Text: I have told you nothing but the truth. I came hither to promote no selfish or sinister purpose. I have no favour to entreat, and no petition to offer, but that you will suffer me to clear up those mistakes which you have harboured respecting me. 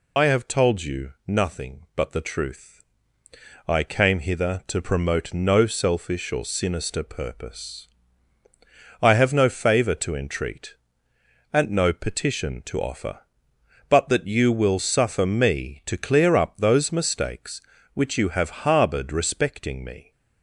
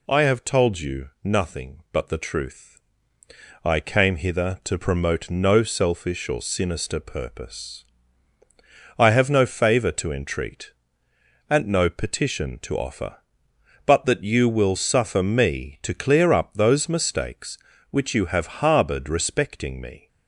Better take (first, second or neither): second